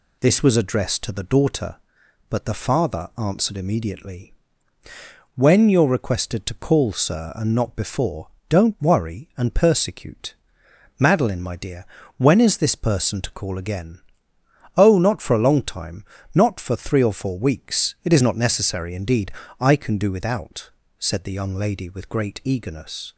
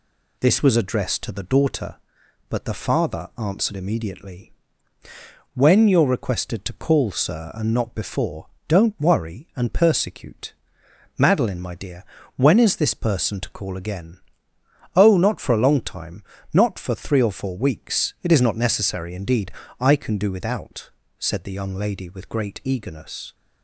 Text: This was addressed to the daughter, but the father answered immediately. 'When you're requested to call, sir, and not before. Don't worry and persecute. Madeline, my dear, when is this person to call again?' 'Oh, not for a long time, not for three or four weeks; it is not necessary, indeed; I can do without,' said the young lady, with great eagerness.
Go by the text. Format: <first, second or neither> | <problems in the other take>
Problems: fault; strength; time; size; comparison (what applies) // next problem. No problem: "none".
neither | none